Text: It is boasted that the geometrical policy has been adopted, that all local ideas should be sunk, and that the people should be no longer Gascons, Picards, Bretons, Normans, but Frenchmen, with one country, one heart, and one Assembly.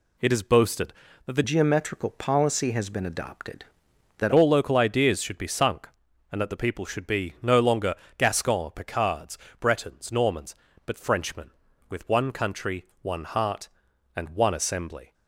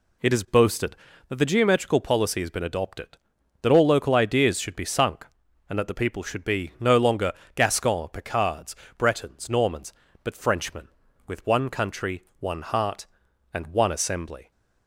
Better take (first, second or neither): second